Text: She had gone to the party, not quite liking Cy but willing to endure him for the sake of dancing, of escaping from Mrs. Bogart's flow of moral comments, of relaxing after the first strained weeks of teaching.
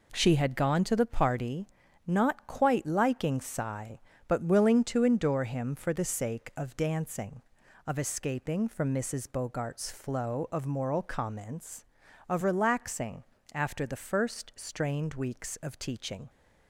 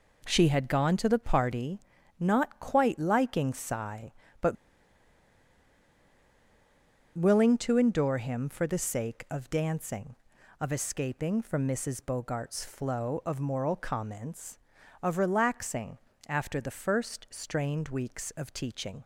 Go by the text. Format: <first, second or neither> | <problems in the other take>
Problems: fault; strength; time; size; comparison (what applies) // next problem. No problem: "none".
first | pauses between "but" and "willing"; strong; at 4.5 s; 2.6 s long // pauses between "relaxing" and "after"; slight; at 15.9 s; 0.32 s long; slight in the first